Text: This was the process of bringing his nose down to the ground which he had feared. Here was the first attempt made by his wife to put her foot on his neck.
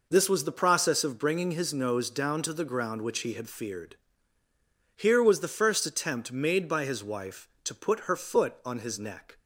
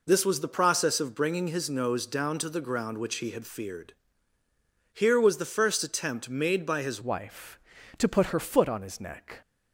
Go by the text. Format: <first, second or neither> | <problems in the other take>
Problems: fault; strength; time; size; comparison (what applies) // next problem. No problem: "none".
first | changes voice at "wife"; from 7.0 s on; 2.4 s long